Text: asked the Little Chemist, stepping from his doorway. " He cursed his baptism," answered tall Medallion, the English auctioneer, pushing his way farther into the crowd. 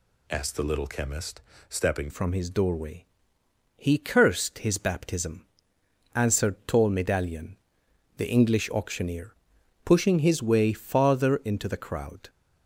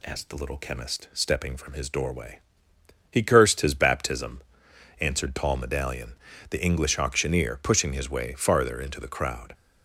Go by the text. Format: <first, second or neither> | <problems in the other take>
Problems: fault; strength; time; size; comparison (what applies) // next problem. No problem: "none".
second | changes voice at "from"; from 2.1 s on; 10.1 s long